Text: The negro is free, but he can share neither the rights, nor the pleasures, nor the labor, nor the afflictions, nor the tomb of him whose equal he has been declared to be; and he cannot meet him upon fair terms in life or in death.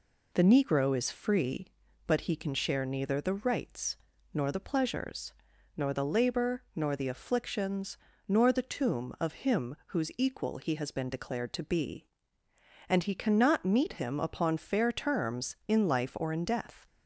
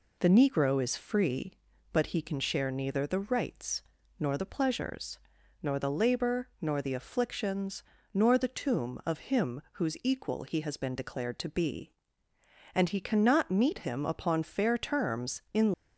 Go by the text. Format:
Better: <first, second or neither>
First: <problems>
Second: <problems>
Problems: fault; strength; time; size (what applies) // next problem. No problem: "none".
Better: first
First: none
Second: stops before "life or in death"; at 15.7 s